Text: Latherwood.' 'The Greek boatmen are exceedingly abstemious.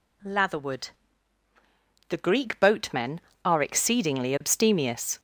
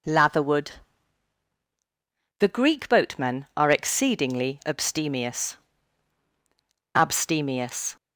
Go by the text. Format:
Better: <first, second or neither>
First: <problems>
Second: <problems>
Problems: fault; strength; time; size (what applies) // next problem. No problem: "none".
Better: first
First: none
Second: says "abstemious" twice; at 6.9 s